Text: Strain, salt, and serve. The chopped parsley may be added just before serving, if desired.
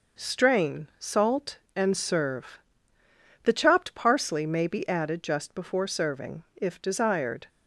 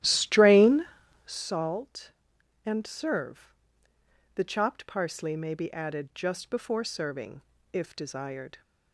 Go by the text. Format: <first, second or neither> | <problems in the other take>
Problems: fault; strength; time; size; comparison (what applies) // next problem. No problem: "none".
first | starts louder than the rest; strong; until 1.5 s; 13 dB